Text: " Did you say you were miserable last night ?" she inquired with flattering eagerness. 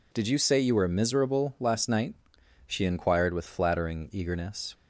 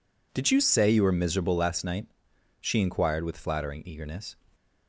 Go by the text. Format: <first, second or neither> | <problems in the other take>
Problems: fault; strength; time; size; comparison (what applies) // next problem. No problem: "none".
neither | none